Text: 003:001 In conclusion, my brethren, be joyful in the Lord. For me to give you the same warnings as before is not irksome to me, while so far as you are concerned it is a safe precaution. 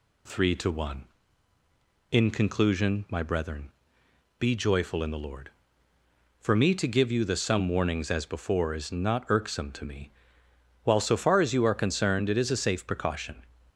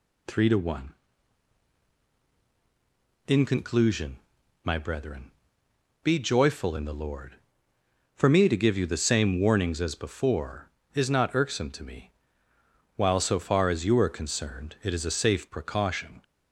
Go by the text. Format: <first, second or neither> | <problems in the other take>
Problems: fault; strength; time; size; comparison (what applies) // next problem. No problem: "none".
second | says "some" for "same"; at 7.3 s